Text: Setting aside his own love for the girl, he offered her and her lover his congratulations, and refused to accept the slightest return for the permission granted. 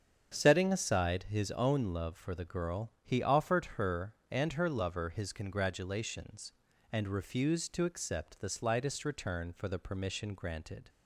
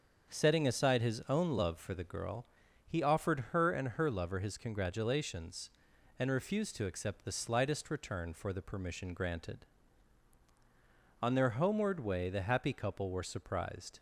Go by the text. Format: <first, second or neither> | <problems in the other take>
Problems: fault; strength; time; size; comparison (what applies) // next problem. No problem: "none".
first | starts louder than the rest; until 1.3 s; 7 dB; strong in the first // goes on to say "On their homeward way the happy couple were surprised"; strong; from 11.2 s on; 2.7 s long